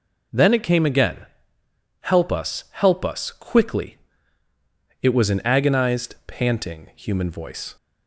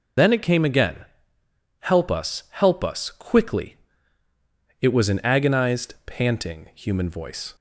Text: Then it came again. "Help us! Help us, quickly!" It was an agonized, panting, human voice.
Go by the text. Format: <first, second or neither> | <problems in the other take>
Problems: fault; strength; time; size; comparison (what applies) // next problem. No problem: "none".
first | loses the start of "Then"; at 0.1 s; 65 ms